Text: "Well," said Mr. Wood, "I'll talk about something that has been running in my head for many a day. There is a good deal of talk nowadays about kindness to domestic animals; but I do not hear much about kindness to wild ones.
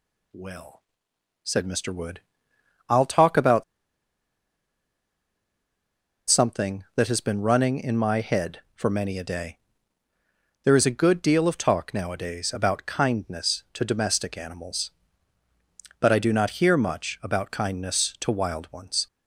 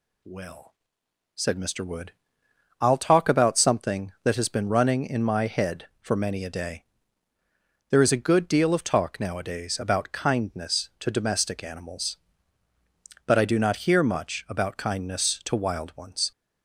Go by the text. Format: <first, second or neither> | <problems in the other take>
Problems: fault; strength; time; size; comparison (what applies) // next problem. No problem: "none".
second | pauses between "about" and "something"; strong; at 3.6 s; 2.6 s long